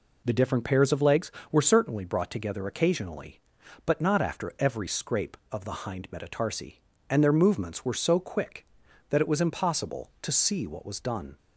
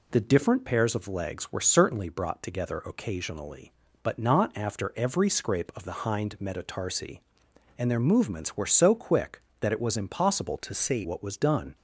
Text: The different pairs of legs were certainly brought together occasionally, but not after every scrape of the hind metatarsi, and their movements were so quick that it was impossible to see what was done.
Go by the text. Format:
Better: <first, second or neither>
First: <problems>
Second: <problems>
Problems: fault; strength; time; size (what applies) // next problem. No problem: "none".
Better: first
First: none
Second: changes voice from "to" to "see"; from 10.5 to 11.0 s; 0.5 s long